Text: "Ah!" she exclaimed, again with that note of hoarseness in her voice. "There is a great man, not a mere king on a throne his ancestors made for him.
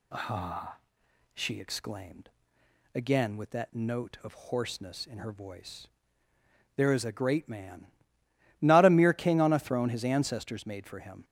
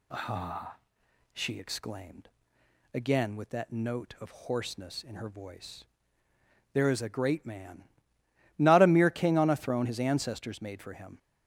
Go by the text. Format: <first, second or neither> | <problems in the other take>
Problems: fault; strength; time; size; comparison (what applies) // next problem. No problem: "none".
neither | none